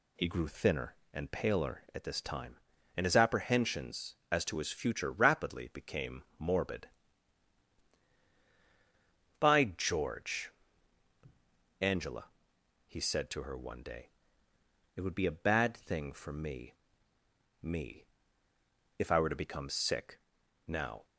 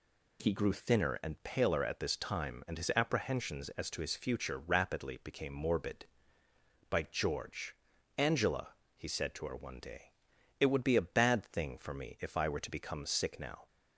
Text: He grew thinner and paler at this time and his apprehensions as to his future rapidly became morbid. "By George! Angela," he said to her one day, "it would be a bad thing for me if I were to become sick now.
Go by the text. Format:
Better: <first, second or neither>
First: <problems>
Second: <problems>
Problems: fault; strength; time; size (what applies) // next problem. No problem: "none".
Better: second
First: pauses between "became" and "morbid"; slight; at 6.2 s; 0.16 s long // says "me" twice; at 17.6 s // pauses between "sick" and "now"; noticeable; at 20.1 s; 0.48 s long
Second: none